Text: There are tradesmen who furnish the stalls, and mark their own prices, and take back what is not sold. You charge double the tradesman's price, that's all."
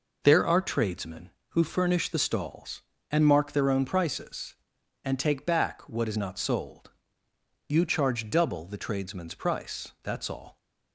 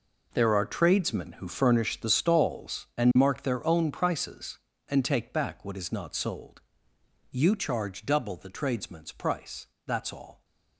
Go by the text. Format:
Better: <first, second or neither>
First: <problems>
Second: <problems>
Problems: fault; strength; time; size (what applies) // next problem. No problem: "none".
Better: first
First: none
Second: gets quieter; strong; throughout; 13 dB